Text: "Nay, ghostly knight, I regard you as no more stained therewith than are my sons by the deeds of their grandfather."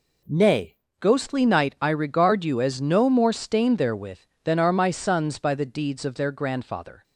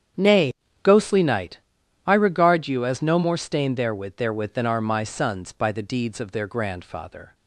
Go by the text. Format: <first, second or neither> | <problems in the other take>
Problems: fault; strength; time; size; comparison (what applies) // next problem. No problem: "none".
first | starts louder than the rest; strong; until 1.4 s; 8.5 dB // says "therewith" twice; at 4.1 s